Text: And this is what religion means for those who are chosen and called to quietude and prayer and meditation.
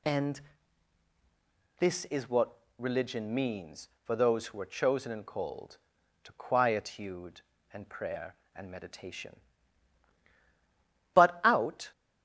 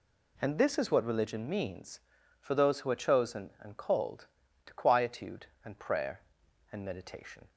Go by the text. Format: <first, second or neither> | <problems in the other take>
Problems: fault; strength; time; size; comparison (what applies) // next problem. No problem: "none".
second | pauses between "And" and "this"; strong; at 0.3 s; 1.3 s long // pauses between "what" and "religion"; slight; at 2.5 s; 0.20 s long // goes on to say "But out"; noticeable; from 11.1 s on; 0.78 s long